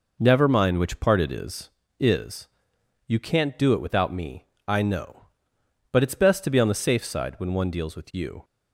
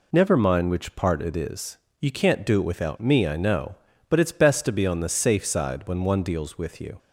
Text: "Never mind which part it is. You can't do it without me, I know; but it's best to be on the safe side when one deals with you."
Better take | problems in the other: second | says "is" twice; at 1.9 s

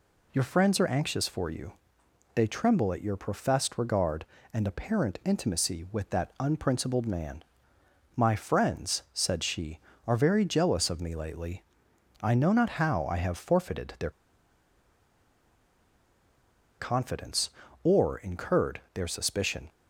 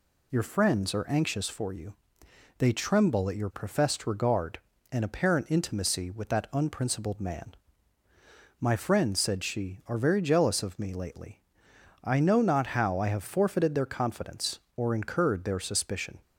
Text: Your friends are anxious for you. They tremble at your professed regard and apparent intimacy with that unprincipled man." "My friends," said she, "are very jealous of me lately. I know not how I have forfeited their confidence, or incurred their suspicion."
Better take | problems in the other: second | pauses between "their" and "confidence"; strong; at 14.1 s; 2.6 s long

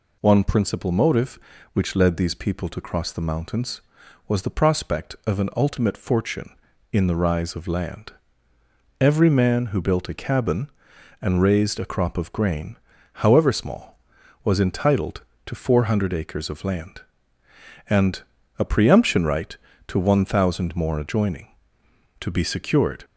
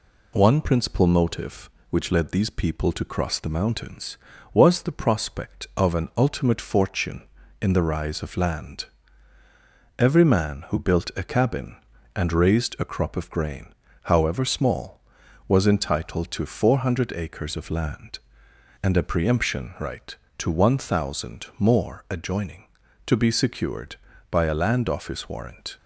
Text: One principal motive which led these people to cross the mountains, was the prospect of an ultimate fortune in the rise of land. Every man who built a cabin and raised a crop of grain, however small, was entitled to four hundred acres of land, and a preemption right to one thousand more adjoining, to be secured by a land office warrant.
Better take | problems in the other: second | pauses between "and" and "a"; slight; at 18.2 s; 0.36 s long // stops before "by a land office warrant"; at 23.0 s

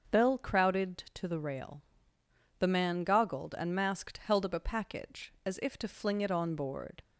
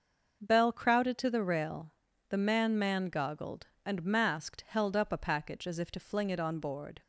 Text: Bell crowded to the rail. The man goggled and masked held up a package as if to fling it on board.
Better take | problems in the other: first | starts louder than the rest; until 1.4 s; 6 dB; also in the first // says "man" twice; at 2.7 s

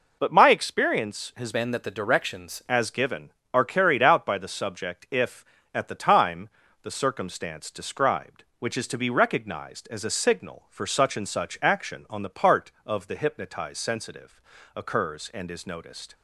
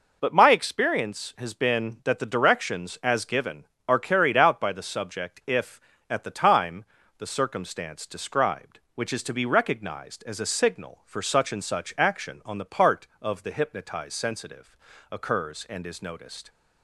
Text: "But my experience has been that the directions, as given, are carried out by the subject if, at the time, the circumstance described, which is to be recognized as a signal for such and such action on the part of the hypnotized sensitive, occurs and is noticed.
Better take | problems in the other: second | changes voice from "been" to "directions"; from 1.5 to 2.6 s; 1.1 s long

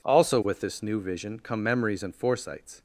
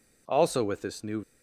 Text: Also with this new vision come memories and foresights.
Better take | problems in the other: first | stops before "vision come memories and foresights"; at 1.2 s

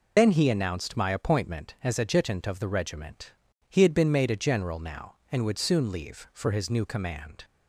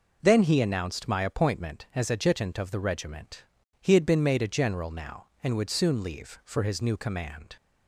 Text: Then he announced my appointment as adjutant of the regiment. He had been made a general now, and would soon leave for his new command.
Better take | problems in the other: second | loses the start of "Then"; at 0.1 s; 65 ms

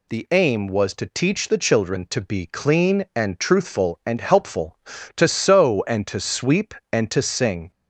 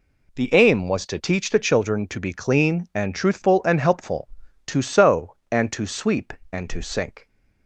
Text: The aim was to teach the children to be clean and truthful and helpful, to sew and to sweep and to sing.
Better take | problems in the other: first | says "sink" for "sing"; at 6.8 s

